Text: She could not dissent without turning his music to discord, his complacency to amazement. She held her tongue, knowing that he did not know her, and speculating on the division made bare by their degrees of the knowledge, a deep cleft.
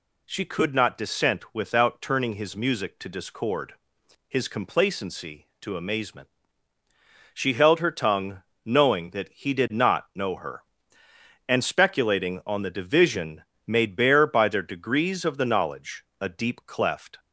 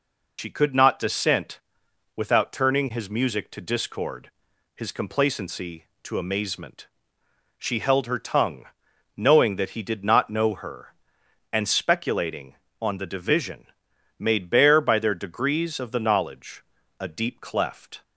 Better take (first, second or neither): first